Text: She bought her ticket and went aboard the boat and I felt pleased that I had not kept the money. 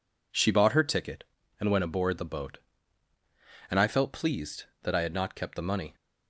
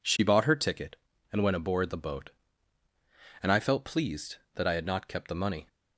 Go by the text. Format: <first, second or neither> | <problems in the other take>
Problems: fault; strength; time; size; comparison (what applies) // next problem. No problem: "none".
neither | none